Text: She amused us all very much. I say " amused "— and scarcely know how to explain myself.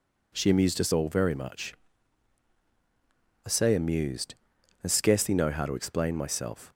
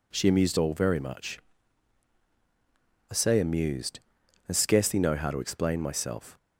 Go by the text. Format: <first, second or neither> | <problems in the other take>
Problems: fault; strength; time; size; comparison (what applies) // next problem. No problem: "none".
first | skips "us"; at 0.5 s